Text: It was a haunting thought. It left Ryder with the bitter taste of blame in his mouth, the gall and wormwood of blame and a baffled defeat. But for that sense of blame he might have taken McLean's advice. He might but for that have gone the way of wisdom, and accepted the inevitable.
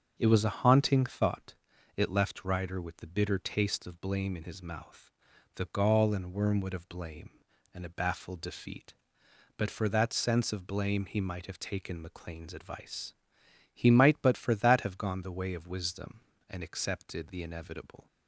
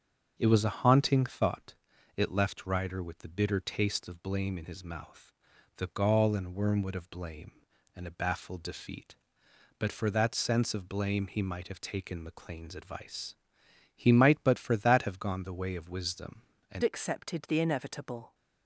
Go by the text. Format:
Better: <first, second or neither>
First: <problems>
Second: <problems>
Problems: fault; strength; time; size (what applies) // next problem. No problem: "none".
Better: first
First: starts louder than the rest; until 1.1 s; 6.5 dB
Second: starts louder than the rest; until 1.3 s; 6.5 dB // changes voice at "accepted"; from 16.8 s on; 1.5 s long